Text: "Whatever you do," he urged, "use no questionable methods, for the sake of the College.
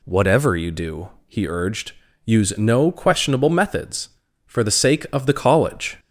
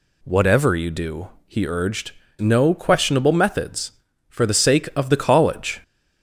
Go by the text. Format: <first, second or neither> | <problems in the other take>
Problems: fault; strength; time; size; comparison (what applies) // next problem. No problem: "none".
first | skips "use"; at 2.2 s